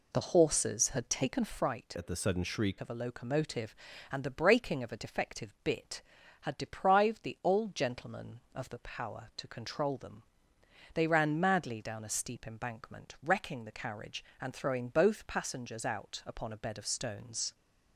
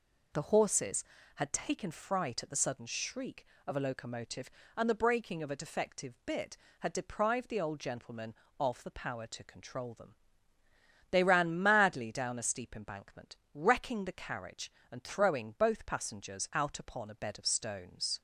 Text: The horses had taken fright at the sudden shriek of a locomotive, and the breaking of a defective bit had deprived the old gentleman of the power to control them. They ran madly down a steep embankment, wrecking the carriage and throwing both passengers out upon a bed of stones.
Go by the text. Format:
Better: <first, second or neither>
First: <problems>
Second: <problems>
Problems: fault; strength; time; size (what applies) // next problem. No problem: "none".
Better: second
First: changes voice from "at" to "shriek"; from 1.9 to 2.7 s; 0.8 s long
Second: none